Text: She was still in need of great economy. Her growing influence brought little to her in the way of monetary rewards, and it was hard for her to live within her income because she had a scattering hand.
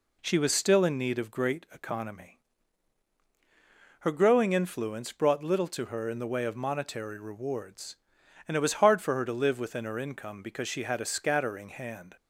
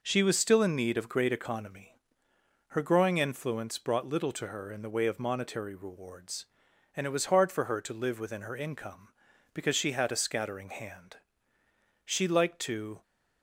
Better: first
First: none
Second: goes on to say "She liked to"; noticeable; from 12.0 s on; 0.98 s long

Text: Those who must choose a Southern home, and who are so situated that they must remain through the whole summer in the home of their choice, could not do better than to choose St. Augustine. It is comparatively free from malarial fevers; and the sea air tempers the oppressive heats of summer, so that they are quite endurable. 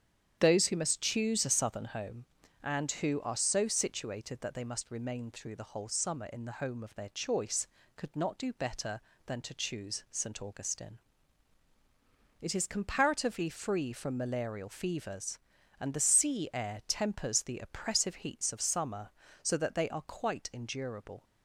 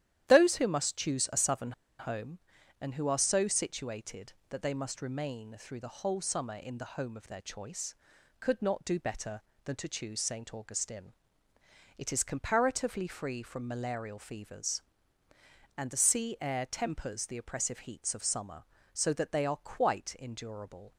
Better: first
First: starts louder than the rest; strong; until 1.4 s; 9 dB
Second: starts louder than the rest; strong; until 1.2 s; 11.5 dB // pauses between "Southern" and "home"; slight; at 1.7 s; 0.26 s long

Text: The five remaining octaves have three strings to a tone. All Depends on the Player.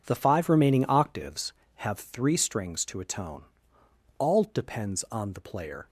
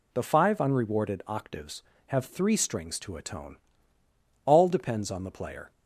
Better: first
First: none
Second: says "unrewarded" for "remaining"; at 0.5 s

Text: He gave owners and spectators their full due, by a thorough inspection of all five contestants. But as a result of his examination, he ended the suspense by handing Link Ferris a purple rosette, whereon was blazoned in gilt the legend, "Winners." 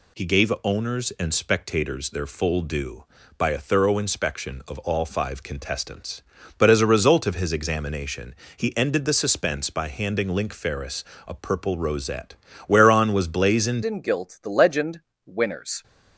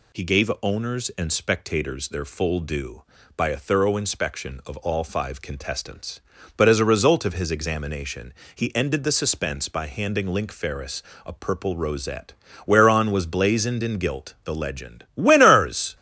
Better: second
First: pauses between "Ferris" and "a"; slight; at 11.0 s; 0.22 s long // changes voice at "in"; from 13.8 s on; 2.0 s long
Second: pauses between "Ferris" and "a"; slight; at 11.0 s; 0.22 s long

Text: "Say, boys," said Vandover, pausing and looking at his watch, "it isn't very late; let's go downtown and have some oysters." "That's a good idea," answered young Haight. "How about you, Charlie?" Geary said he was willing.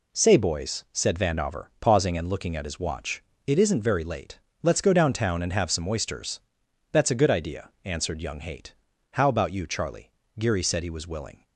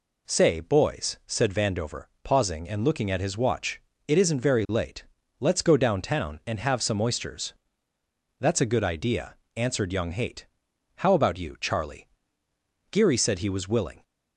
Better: neither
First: none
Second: none

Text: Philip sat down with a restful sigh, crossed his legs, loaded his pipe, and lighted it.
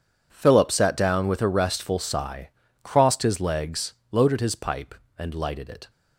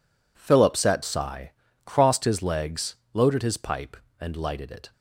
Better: first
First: none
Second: skips "down with a restful"; at 1.0 s

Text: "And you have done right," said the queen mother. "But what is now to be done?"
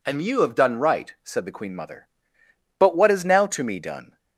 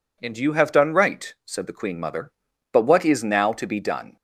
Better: second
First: says "me" for "be"; at 3.6 s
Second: none

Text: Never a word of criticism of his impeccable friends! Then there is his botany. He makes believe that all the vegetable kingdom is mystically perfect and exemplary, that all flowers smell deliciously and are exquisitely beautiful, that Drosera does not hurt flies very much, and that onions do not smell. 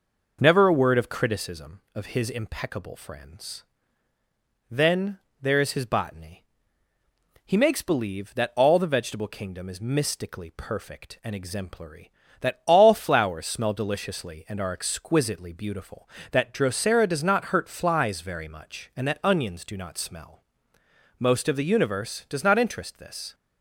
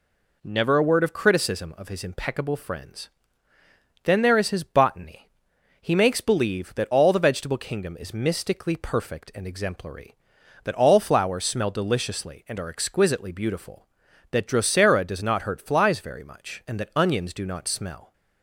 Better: second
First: pauses between "Then" and "there"; slight; at 5.1 s; 0.22 s long // goes on to say "Most of the universe does not interest this"; strong; from 21.1 s on; 2.1 s long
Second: none

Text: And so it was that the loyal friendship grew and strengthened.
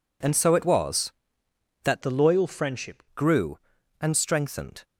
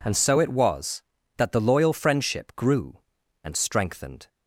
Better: second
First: changes voice from "the" to "friendship"; from 2.0 to 3.0 s; 1.0 s long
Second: none

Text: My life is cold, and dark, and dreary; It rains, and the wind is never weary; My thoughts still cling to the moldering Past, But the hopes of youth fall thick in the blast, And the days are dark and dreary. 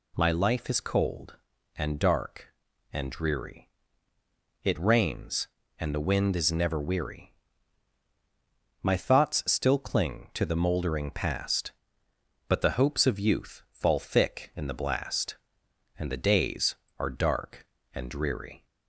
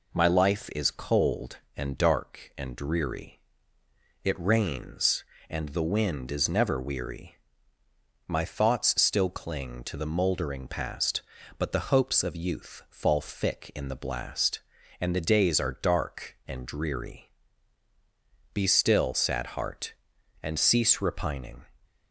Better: first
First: none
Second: goes on to say "Be still sad heart and cease repining"; strong; from 18.5 s on; 3.1 s long

